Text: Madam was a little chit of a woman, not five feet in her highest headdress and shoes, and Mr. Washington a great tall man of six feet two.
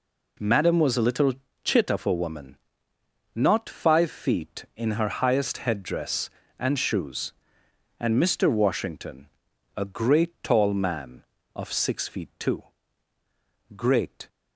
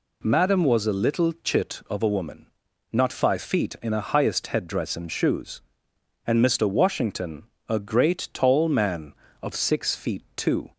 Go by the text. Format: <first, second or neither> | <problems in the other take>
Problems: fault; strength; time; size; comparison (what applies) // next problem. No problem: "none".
second | pauses between "little" and "chit"; slight; at 1.3 s; 0.32 s long // pauses between "Washington" and "a"; noticeable; at 9.2 s; 0.50 s long; slight in the second // goes on to say "Great"; from 13.7 s on; 0.54 s long